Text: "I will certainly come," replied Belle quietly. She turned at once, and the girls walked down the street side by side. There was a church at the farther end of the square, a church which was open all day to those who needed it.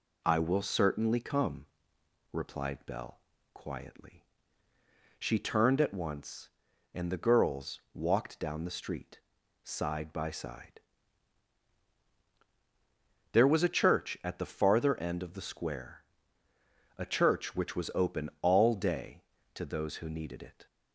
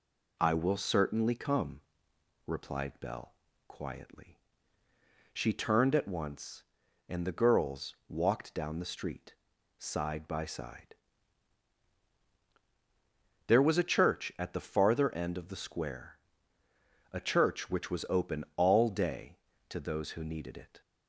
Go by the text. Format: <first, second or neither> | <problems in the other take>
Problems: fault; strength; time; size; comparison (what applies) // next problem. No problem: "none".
neither | pauses between "Belle" and "quietly"; slight; the same in both // pauses between "street" and "side"; the same in both